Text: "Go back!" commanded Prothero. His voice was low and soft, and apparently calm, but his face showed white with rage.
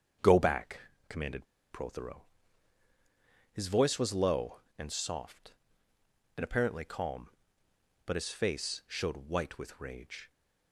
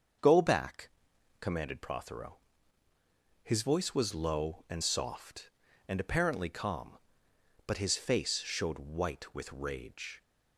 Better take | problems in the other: second | starts louder than the rest; strong; until 1.7 s; 8 dB; also in the second // pauses between "commanded" and "Prothero"; slight; at 1.4 s; 0.26 s long

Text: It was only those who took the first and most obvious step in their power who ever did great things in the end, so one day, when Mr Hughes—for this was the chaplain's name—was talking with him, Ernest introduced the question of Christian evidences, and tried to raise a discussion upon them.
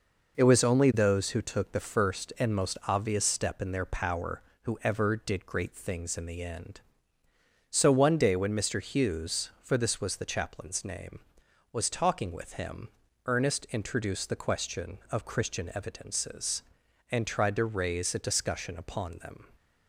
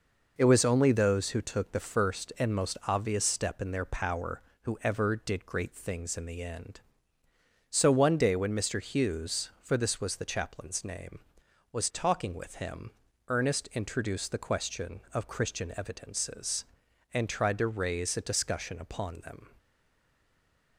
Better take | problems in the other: first | stays silent after the last word; noticeable; from 19.5 s on; 1.2 s long

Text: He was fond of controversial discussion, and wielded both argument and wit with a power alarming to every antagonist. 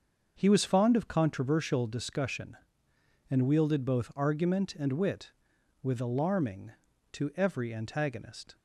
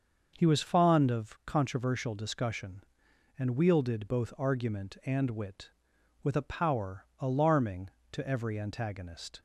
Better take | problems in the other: second | starts louder than the rest; until 1.3 s; 6.5 dB; also in the second // skips "a power"; at 5.9 s

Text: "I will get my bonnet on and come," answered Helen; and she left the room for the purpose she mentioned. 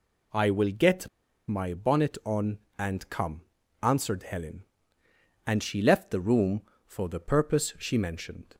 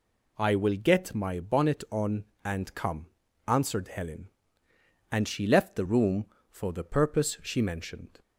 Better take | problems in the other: second | pauses between "get" and "my"; at 1.0 s; 0.40 s long

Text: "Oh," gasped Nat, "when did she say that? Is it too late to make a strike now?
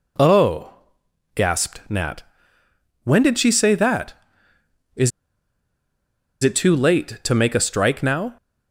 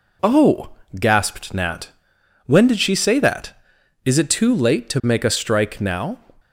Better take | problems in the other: second | pauses between "Is" and "it"; strong; at 5.1 s; 1.3 s long

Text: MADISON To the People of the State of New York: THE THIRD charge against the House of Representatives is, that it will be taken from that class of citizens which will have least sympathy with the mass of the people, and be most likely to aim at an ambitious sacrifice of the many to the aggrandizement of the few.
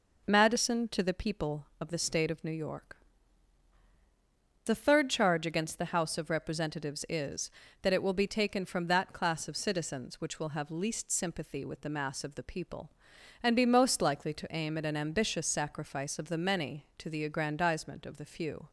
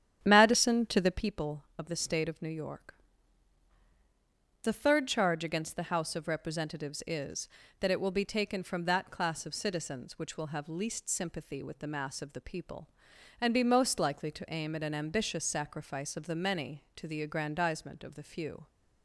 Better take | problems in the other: first | starts louder than the rest; strong; until 1.4 s; 9.5 dB

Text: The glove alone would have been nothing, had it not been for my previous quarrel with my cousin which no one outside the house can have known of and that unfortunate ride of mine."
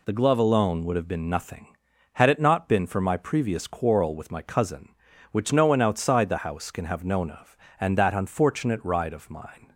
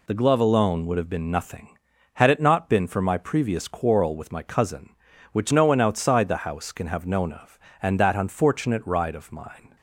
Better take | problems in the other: neither | none

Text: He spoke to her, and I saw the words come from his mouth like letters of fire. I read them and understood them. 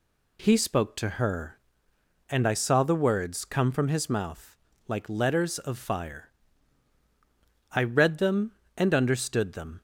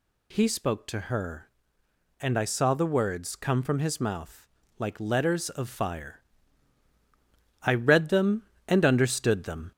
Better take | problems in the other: first | gets louder; slight; throughout; 2 dB // pauses between "mouth" and "like"; slight; at 4.4 s; 0.32 s long; slight in the first

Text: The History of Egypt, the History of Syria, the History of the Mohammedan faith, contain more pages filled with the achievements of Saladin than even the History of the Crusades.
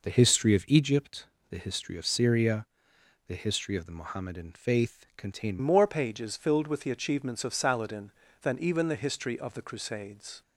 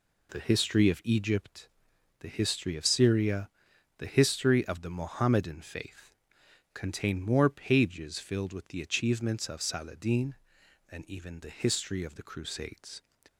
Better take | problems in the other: second | changes voice at "more"; from 5.6 s on; 4.8 s long

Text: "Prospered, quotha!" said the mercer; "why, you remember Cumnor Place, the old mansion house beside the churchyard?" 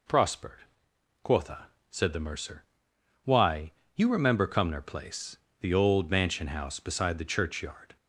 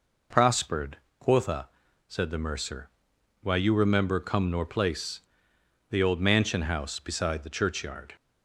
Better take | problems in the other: neither | none

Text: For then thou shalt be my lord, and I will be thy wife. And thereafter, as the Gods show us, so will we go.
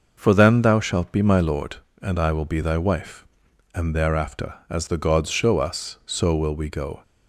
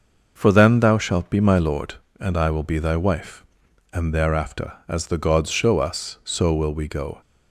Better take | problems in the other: neither | none

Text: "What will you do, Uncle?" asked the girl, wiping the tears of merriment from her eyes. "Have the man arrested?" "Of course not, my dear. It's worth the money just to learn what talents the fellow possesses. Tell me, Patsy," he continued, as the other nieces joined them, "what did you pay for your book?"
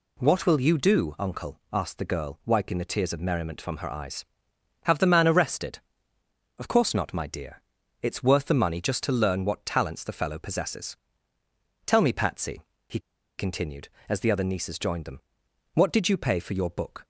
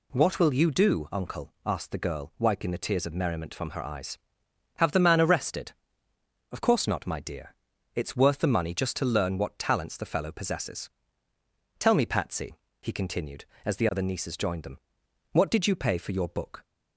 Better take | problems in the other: second | pauses between "he" and "continued"; at 12.9 s; 0.39 s long

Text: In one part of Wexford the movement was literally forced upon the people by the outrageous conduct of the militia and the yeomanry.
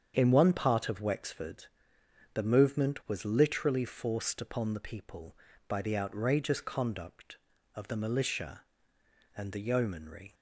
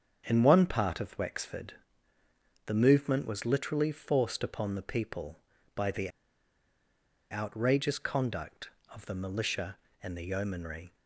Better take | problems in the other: first | starts louder than the rest; strong; until 1.2 s; 7.5 dB; strong in the first // pauses between "Wexford" and "the"; noticeable; at 1.7 s; 0.90 s long; noticeable in the first // pauses between "the" and "outrageous"; at 6.0 s; 1.2 s long

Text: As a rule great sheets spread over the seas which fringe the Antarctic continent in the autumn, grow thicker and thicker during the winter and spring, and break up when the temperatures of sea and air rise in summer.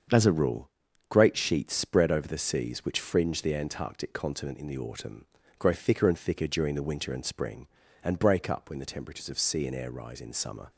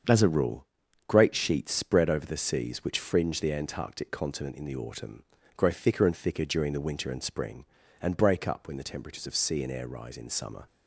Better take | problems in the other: neither | starts louder than the rest; the same in both // pauses between "rule" and "great"; the same in both

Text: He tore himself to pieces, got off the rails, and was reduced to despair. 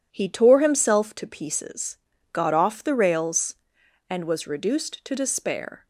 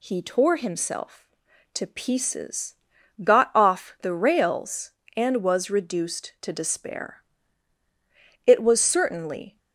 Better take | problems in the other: first | goes on to say "It was certainly"; noticeable; from 8.4 s on; 1.1 s long

